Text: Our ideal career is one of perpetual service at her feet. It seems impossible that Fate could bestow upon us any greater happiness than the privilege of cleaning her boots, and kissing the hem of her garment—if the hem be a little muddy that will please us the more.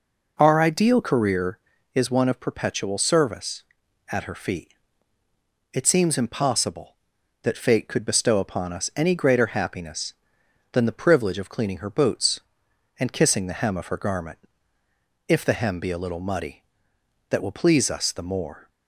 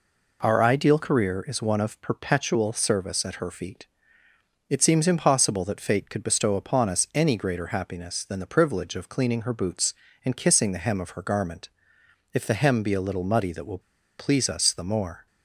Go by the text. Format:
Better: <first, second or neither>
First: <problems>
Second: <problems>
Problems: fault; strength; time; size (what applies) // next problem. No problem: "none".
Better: first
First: none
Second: pauses between "will" and "please"; at 13.7 s; 0.40 s long